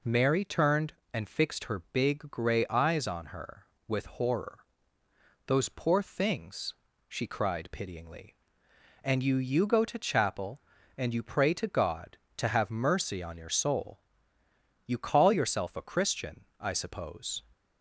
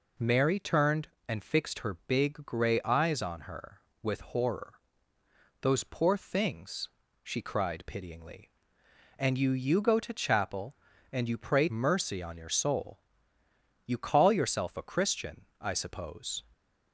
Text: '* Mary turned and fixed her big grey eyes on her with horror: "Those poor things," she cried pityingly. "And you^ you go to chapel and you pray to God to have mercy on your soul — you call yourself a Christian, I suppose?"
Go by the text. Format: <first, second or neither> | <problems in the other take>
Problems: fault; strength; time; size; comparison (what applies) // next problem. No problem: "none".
first | skips "to God to have"; at 11.6 s